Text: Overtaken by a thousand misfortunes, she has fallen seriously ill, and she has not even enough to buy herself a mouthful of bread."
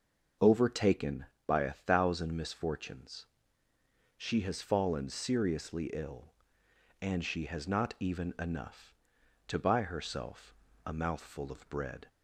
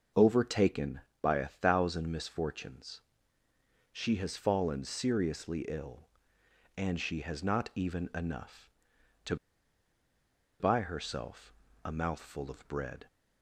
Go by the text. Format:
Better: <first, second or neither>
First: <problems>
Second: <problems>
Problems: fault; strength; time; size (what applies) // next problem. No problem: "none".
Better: first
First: starts louder than the rest; until 1.6 s; 6.5 dB // pauses between "herself" and "a"; slight; at 10.5 s; 0.30 s long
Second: starts louder than the rest; until 1.4 s; 6.5 dB // pauses between "to" and "buy"; at 9.3 s; 1.2 s long // pauses between "herself" and "a"; slight; at 11.5 s; 0.30 s long